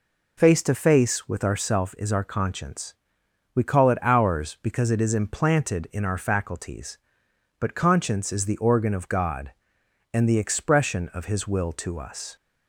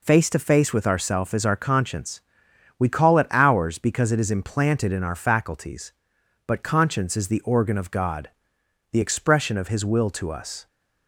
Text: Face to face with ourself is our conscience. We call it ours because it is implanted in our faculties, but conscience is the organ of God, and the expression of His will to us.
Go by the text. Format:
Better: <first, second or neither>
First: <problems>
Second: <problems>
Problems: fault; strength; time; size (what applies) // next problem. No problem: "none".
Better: first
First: none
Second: skips "and"; at 8.6 s